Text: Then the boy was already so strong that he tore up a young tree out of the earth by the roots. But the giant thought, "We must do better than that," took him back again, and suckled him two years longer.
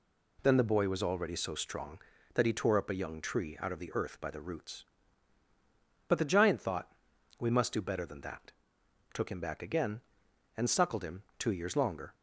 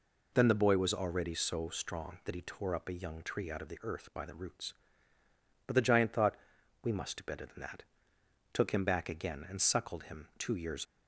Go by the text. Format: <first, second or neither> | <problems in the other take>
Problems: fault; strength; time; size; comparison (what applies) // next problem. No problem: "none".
first | stops before "longer"; at 10.8 s